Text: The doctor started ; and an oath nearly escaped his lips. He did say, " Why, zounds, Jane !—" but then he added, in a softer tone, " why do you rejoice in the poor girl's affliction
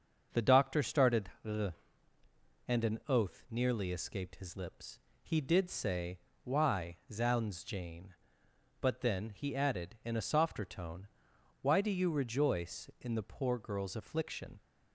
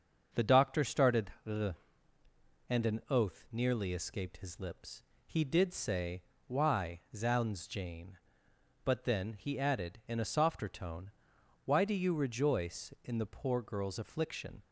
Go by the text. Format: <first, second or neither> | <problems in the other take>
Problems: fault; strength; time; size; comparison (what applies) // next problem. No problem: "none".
neither | starts louder than the rest; strong; the same in both